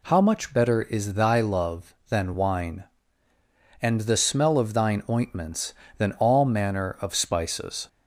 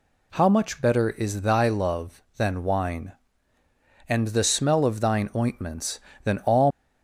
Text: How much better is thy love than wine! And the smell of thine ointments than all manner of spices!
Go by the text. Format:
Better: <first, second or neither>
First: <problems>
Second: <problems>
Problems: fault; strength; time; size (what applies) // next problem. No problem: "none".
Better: first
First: none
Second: stops before "manner of spices"; at 6.6 s